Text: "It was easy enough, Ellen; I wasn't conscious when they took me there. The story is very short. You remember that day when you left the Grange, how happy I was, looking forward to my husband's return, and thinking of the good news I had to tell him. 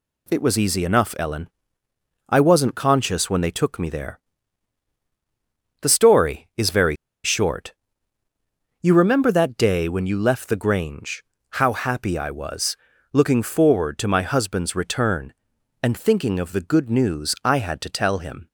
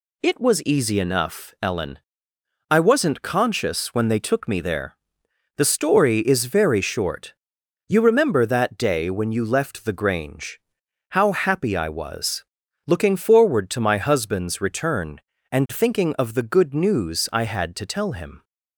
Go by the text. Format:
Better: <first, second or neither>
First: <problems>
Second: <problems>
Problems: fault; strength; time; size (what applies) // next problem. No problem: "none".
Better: second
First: pauses between "very" and "short"; slight; at 6.9 s; 0.28 s long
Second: none